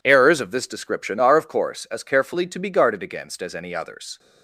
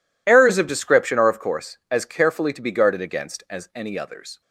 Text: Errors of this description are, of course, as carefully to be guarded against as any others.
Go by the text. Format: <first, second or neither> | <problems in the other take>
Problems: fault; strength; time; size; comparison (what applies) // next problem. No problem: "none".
first | skips "this"; at 0.6 s